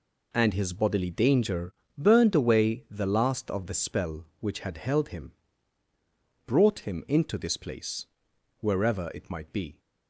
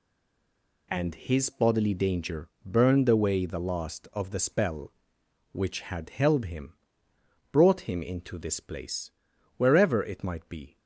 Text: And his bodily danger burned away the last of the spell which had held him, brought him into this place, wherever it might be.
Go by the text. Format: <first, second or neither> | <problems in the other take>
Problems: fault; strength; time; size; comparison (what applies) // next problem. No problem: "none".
first | stays silent before the first word; slight; until 0.9 s; 0.9 s long // pauses between "danger" and "burned"; slight; at 2.4 s; 0.16 s long; slight in the first